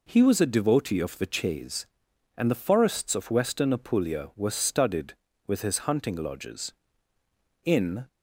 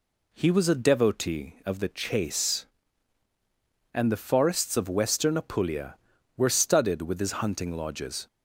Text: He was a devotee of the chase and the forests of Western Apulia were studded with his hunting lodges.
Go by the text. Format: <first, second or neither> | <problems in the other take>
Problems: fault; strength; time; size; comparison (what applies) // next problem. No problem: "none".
second | goes on to say "In"; slight; from 7.6 s on; 0.42 s long